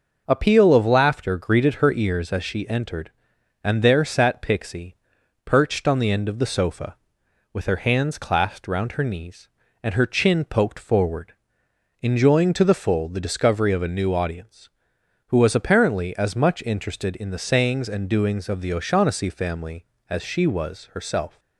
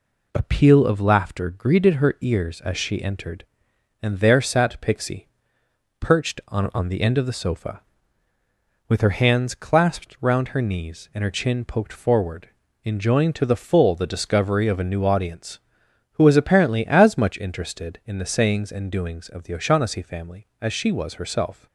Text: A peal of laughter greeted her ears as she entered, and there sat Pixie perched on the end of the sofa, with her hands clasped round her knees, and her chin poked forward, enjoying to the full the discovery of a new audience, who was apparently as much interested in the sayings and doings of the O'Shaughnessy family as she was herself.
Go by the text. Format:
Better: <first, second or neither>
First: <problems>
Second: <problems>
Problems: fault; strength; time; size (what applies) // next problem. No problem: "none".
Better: first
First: pauses between "Pixie" and "perched"; noticeable; at 4.9 s; 0.50 s long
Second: pauses between "Pixie" and "perched"; noticeable; at 5.2 s; 0.72 s long // says "on" twice; at 6.7 s